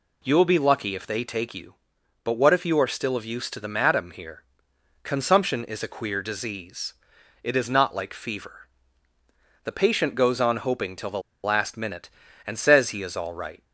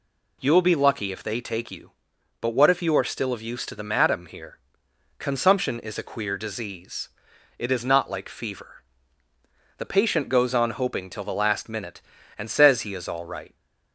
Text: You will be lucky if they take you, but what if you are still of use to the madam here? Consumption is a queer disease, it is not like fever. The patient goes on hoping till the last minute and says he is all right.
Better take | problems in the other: second | pauses between "the" and "last"; slight; at 11.1 s; 0.24 s long

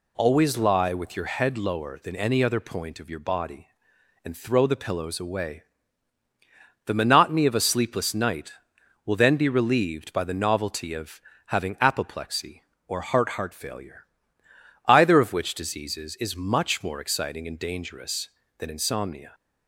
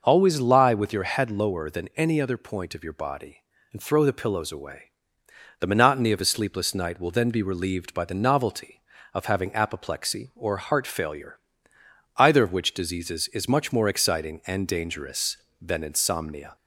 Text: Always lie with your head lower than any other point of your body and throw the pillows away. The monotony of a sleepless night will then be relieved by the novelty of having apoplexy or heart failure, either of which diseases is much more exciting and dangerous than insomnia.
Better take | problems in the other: second | pauses between "of" and "having"; slight; at 11.2 s; 0.26 s long // says "heart" twice; at 13.3 s

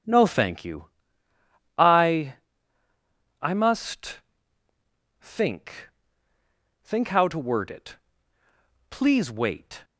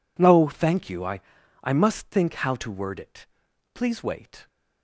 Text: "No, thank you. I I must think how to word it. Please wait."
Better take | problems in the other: second | pauses between "I" and "I"; at 2.3 s; 1.0 s long; also in the second // pauses between "must" and "think"; at 4.1 s; 1.0 s long // says "think" twice; at 6.8 s

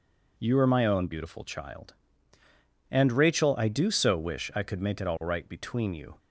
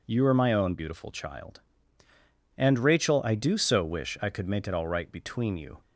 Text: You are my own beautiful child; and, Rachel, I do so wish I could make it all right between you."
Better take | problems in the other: neither | none

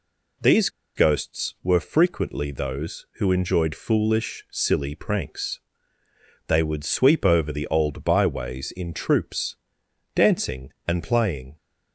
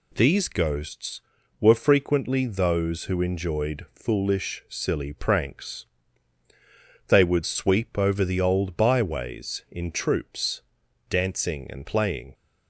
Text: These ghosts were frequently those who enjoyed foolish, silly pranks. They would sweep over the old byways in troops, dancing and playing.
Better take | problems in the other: second | pauses between "These" and "ghosts"; slight; at 0.6 s; 0.27 s long

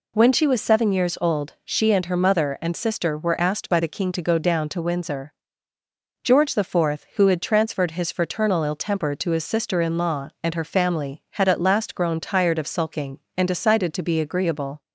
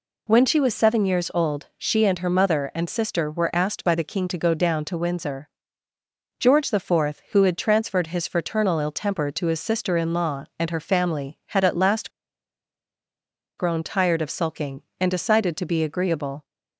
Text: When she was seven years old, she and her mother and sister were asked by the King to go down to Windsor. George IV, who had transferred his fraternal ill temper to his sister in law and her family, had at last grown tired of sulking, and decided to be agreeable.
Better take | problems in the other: first | pauses between "last" and "grown"; strong; at 12.0 s; 1.4 s long

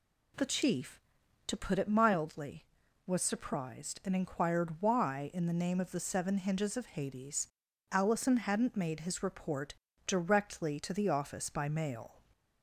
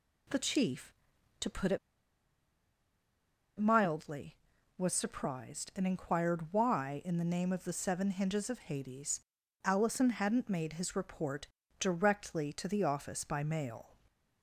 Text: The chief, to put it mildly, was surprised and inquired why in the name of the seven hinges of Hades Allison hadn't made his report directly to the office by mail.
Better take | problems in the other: first | pauses between "it" and "mildly"; strong; at 1.7 s; 1.7 s long // pauses between "Hades" and "Allison"; noticeable; at 9.1 s; 0.46 s long; noticeable in the first // pauses between "report" and "directly"; slight; at 11.4 s; 0.32 s long; slight in the first

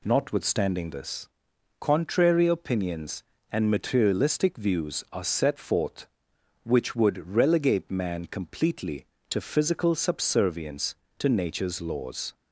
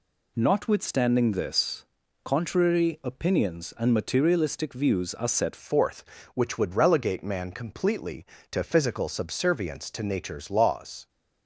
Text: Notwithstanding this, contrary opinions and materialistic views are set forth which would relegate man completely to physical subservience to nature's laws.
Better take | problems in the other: first | changes voice at "forth"; from 5.5 s on; 5.5 s long

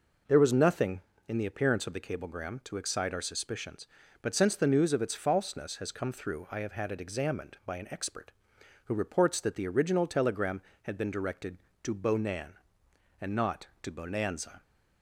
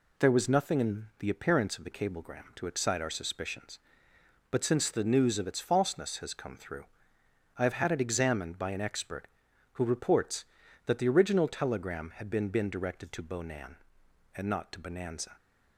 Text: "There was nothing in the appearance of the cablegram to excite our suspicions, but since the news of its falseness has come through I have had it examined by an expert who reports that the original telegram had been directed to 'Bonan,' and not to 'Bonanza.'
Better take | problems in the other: first | pauses between "through" and "I"; noticeable; at 6.8 s; 0.72 s long // says "been" twice; at 12.4 s

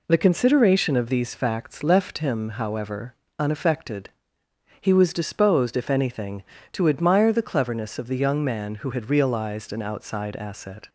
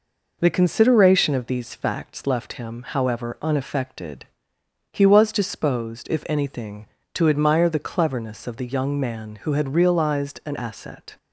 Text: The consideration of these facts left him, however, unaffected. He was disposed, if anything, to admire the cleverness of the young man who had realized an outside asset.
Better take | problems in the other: first | skips "outside"; at 10.5 s

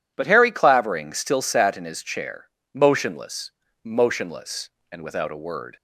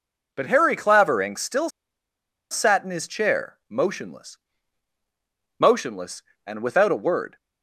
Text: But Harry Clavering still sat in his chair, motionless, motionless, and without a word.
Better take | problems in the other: first | pauses between "still" and "sat"; noticeable; at 1.6 s; 0.82 s long

